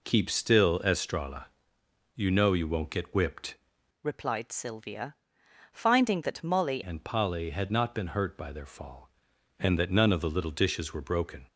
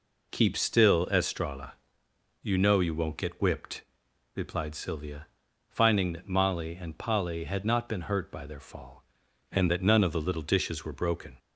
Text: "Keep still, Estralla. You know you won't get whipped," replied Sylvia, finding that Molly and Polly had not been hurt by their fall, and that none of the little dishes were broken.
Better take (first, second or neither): second